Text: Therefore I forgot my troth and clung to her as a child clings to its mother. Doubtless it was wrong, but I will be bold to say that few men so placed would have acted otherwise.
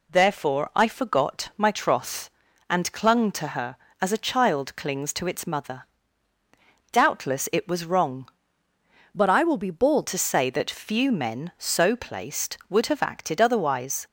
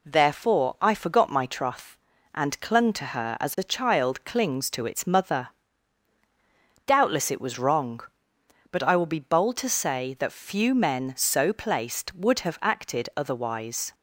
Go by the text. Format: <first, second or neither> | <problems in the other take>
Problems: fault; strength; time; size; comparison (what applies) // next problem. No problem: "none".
second | changes voice from "but" to "bold"; from 9.1 to 10.0 s; 0.9 s long